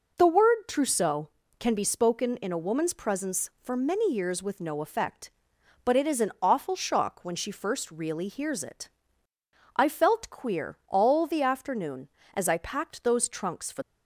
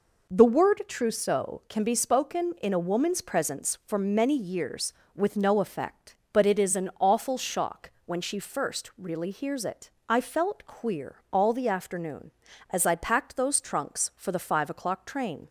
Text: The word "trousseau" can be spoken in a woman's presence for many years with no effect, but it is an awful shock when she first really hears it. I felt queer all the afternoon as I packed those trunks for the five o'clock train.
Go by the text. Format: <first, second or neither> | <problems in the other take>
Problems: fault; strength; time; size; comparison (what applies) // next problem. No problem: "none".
second | stops before "the five o'clock train"; at 13.8 s